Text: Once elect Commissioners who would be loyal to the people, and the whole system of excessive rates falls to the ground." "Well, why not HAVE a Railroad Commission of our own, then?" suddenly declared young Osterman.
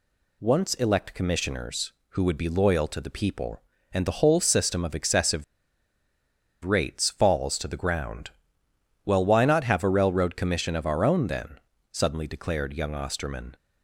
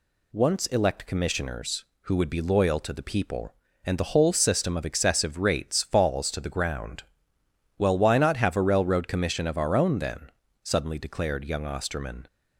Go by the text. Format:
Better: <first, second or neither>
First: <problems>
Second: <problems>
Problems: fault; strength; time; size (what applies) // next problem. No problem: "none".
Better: second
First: pauses between "excessive" and "rates"; at 5.4 s; 1.2 s long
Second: none